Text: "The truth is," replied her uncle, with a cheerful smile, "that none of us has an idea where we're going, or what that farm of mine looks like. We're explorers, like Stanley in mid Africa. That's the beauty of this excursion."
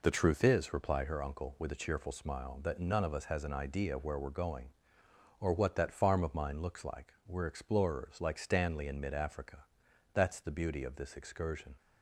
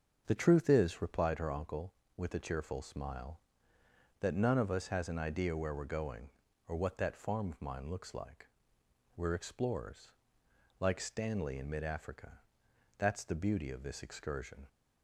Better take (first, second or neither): first